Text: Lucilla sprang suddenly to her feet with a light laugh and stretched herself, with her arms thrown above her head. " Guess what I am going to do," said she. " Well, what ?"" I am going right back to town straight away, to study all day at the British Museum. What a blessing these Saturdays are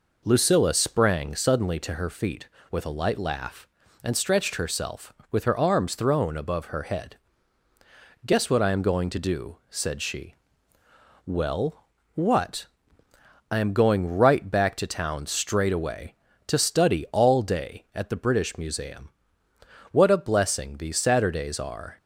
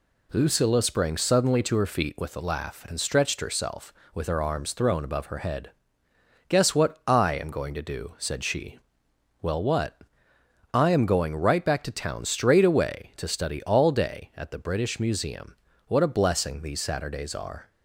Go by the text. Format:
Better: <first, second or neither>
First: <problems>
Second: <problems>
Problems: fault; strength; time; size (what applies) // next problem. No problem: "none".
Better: first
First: none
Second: skips "light"; at 2.4 s